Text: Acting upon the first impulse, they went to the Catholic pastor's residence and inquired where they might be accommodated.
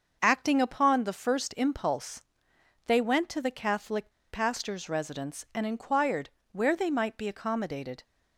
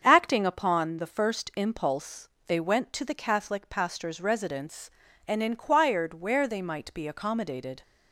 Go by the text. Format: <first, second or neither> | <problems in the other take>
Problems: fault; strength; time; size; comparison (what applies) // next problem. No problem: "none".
second | starts louder than the rest; until 1.2 s; 6.5 dB; strong in the second // pauses between "Catholic" and "pastor's"; slight; at 4.1 s; 0.18 s long // pauses between "inquired" and "where"; slight; at 6.2 s; 0.22 s long